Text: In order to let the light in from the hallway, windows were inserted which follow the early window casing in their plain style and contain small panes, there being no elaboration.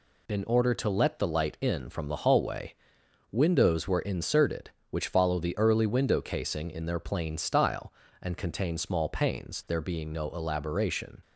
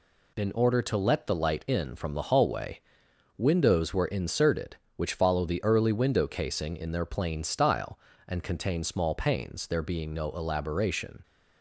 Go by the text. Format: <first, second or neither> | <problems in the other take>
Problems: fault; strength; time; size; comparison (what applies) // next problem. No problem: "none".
neither | none